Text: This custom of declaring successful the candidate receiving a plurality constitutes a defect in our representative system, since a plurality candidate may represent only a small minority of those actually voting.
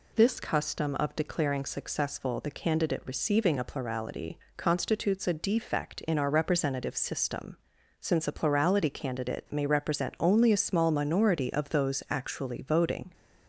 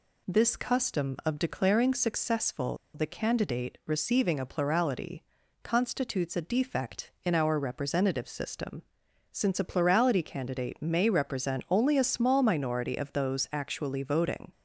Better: first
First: pauses between "plurality" and "constitutes"; slight; at 4.3 s; 0.20 s long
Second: pauses between "successful" and "the"; slight; at 2.7 s; 0.18 s long // pauses between "plurality" and "constitutes"; at 5.2 s; 0.38 s long

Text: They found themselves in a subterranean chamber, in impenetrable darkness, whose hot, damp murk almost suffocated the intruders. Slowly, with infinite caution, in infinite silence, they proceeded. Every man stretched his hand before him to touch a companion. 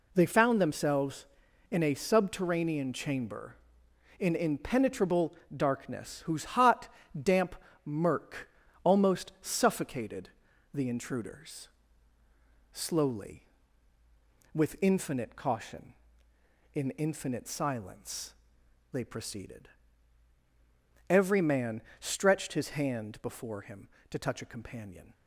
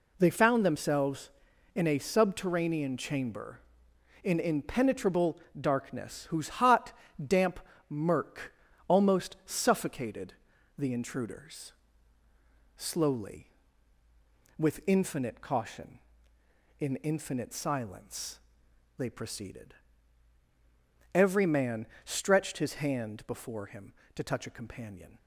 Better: neither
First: pauses between "impenetrable" and "darkness"; slight; at 5.3 s; 0.22 s long // pauses between "damp" and "murk"; slight; at 7.5 s; 0.30 s long // pauses between "murk" and "almost"; slight; at 8.4 s; 0.34 s long // pauses between "suffocated" and "the"; at 10.2 s; 0.44 s long // pauses between "man" and "stretched"; slight; at 21.8 s; 0.16 s long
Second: pauses between "impenetrable" and "darkness"; slight; at 5.3 s; 0.22 s long // pauses between "damp" and "murk"; slight; at 7.5 s; 0.30 s long // pauses between "murk" and "almost"; slight; at 8.5 s; 0.34 s long // pauses between "suffocated" and "the"; at 10.3 s; 0.44 s long // pauses between "man" and "stretched"; slight; at 21.8 s; 0.16 s long

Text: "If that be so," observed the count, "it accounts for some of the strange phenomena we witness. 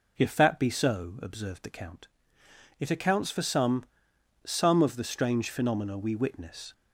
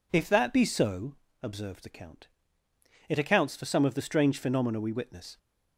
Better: second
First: says "some" twice; at 4.4 s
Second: none

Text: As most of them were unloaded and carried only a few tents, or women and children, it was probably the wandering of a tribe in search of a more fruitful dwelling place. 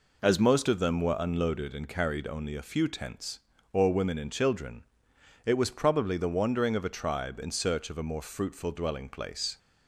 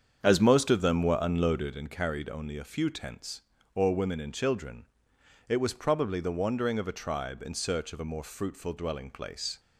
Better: first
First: none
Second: starts louder than the rest; strong; until 1.8 s; 7.5 dB

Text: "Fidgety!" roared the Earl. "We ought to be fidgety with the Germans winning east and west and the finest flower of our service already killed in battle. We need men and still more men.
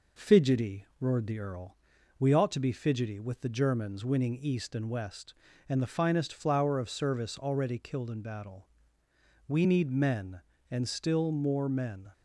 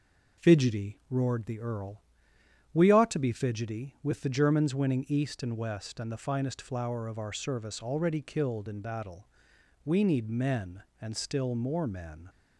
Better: second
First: skips "our"; at 6.8 s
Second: none

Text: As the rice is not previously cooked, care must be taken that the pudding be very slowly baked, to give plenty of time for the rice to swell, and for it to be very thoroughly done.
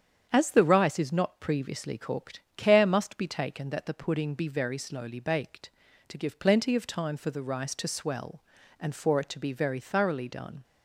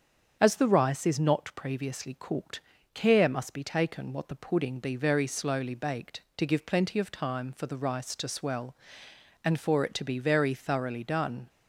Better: first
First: starts louder than the rest; strong; until 1.3 s; 8 dB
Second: starts louder than the rest; strong; until 1.4 s; 7.5 dB // says "what" for "that"; at 4.1 s

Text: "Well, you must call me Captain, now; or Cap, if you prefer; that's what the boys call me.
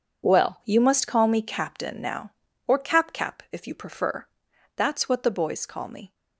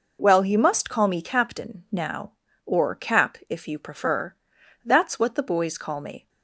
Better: second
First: says "Cap" twice; at 3.1 s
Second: none

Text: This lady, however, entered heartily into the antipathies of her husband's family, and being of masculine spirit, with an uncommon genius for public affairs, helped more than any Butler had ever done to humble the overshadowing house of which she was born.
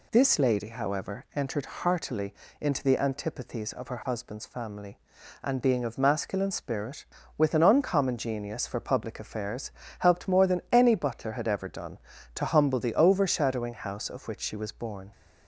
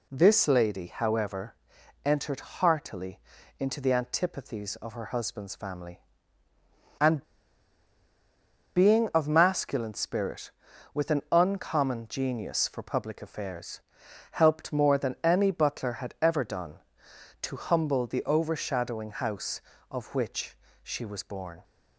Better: first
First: pauses between "heartily" and "into"; slight; at 2.3 s; 0.28 s long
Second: pauses between "heartily" and "into"; at 3.1 s; 0.40 s long // pauses between "and" and "being"; strong; at 7.2 s; 1.5 s long // pauses between "which" and "she"; slight; at 20.5 s; 0.24 s long

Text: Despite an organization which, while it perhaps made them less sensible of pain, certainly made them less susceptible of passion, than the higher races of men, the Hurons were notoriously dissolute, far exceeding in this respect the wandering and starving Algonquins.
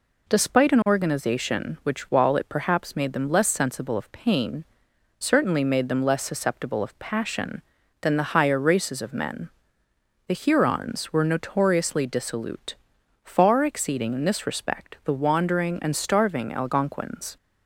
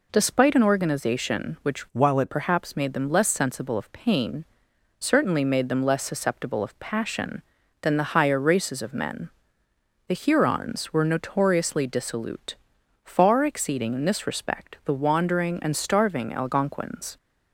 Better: first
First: none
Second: changes voice from "while" to "it"; from 1.9 to 2.3 s; 0.4 s long

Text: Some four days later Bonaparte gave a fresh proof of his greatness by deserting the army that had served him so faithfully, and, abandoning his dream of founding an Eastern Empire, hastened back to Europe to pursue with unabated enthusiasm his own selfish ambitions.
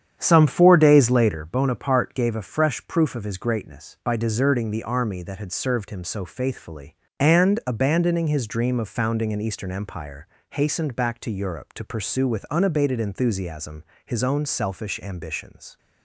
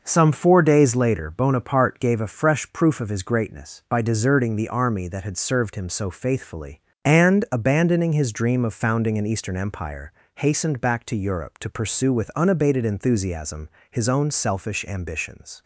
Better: second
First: starts louder than the rest; strong; until 1.4 s; 9 dB // pauses between "enthusiasm" and "his"; slight; at 13.8 s; 0.20 s long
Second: pauses between "enthusiasm" and "his"; slight; at 13.7 s; 0.20 s long

